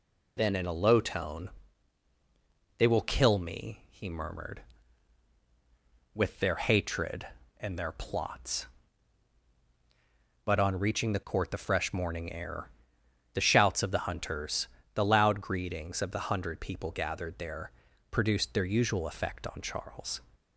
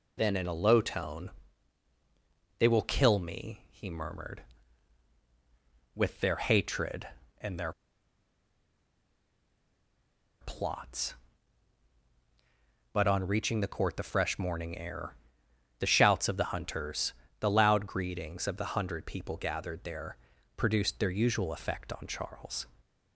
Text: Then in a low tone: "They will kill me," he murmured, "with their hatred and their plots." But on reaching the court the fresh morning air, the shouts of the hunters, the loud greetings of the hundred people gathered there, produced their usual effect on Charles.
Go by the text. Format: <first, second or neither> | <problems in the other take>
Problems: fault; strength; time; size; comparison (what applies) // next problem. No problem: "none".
first | pauses between "their" and "plots"; strong; at 7.7 s; 2.7 s long